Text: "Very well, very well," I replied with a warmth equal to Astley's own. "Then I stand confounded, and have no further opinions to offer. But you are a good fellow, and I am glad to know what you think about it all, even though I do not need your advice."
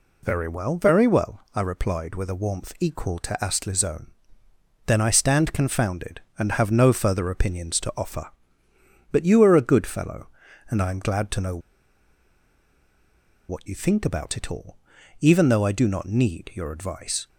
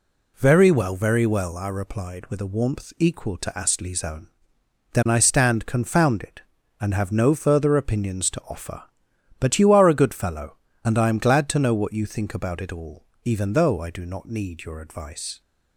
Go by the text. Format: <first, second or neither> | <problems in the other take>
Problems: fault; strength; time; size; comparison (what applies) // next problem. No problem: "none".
second | pauses between "know" and "what"; strong; at 11.5 s; 1.9 s long